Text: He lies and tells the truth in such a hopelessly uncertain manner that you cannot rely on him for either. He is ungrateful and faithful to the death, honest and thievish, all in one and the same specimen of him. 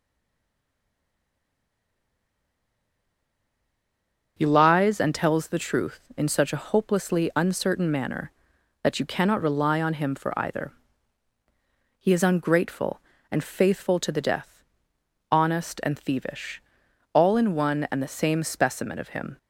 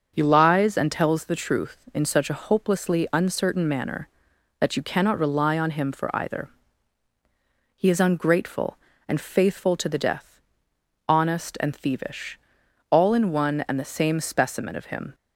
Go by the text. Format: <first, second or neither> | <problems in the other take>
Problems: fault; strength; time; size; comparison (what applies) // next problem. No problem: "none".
second | stays silent before the first word; strong; until 4.3 s; 4.3 s long // starts louder than the rest; noticeable; until 5.3 s; 6 dB; noticeable in the second